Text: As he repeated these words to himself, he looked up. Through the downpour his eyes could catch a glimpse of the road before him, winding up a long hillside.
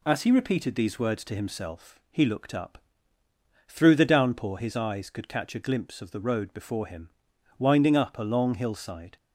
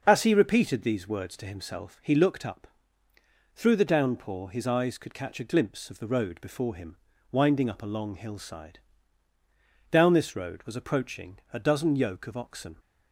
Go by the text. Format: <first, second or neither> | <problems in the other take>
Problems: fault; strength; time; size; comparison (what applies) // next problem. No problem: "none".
first | starts louder than the rest; until 1.0 s; 6.5 dB // goes on to say "Down this road was approaching a dozen yoke of oxen"; strong; from 9.9 s on; 2.8 s long